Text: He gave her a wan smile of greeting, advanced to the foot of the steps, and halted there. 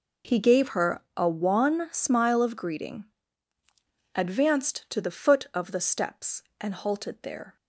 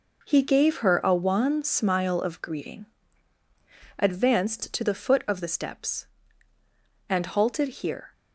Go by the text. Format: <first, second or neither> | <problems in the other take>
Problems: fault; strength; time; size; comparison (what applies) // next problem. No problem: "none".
first | says "here" for "there"; at 7.6 s